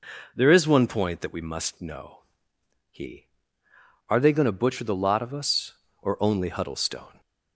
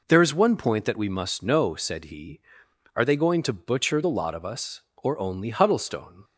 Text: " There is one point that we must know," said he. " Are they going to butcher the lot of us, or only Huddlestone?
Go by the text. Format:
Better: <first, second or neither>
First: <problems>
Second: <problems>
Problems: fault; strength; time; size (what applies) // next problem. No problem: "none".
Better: second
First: skips "said"; at 2.5 s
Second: none